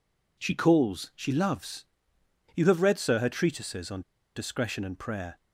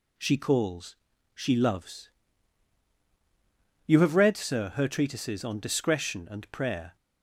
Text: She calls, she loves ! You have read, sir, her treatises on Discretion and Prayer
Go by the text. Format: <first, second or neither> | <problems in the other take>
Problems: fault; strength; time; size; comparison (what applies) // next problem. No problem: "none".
second | pauses between "on" and "Discretion"; slight; at 4.0 s; 0.34 s long